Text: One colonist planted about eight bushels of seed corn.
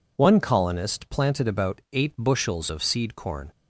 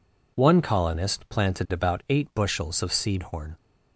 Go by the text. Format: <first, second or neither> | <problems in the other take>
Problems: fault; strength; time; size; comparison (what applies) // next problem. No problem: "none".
first | says "horn" for "corn"; at 3.2 s